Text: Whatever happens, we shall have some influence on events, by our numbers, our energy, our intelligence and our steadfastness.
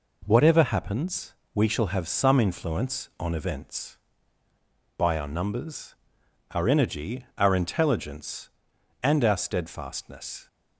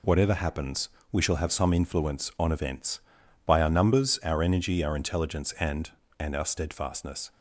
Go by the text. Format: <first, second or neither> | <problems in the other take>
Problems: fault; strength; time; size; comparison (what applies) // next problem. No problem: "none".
first | says "and" twice; at 6.1 s